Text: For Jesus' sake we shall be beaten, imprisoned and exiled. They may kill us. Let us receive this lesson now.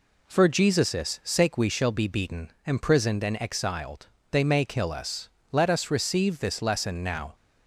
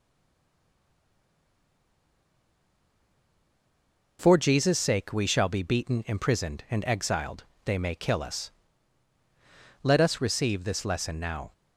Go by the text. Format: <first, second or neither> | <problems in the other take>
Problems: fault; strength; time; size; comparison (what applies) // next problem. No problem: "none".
first | stays silent before the first word; strong; until 4.1 s; 4.1 s long